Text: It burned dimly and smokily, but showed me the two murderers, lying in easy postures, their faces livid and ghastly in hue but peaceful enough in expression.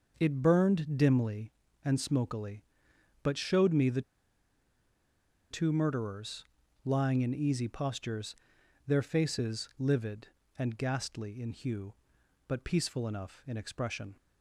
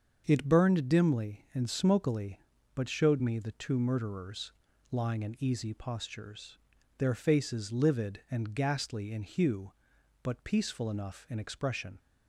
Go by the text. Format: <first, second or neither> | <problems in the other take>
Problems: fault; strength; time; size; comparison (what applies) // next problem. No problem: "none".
second | starts louder than the rest; noticeable; until 1.2 s; 6 dB; also in the second // pauses between "the" and "two"; strong; at 4.0 s; 1.4 s long